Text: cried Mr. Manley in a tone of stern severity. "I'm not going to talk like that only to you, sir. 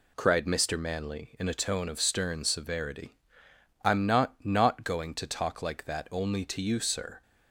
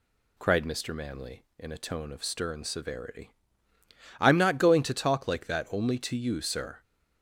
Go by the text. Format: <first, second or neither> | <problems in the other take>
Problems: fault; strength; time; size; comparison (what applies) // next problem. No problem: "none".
second | says "not" twice; at 4.4 s